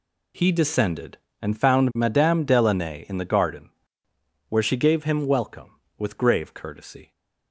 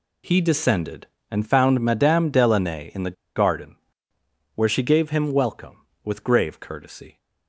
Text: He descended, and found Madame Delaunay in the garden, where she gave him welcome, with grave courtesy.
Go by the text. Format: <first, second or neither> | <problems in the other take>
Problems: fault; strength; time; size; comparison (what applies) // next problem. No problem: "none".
first | pauses between "the" and "garden"; slight; at 3.1 s; 0.22 s long